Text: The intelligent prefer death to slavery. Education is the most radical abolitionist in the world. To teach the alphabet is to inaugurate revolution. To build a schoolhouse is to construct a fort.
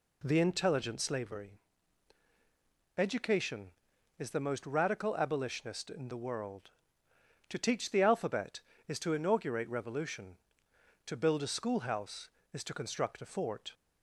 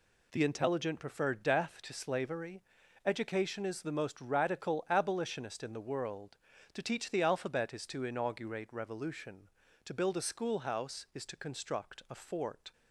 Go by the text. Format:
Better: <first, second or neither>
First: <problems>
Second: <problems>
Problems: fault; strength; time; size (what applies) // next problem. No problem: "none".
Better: second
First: skips "prefer death to"; at 1.0 s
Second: none